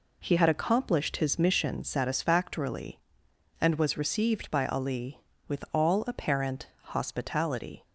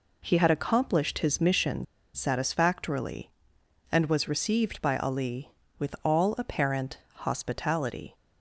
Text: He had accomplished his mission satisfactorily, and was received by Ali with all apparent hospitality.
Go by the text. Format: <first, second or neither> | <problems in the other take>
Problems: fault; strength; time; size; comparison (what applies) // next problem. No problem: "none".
first | pauses between "mission" and "satisfactorily"; slight; at 1.8 s; 0.29 s long // pauses between "apparent" and "hospitality"; slight; at 6.9 s; 0.16 s long; slight in the first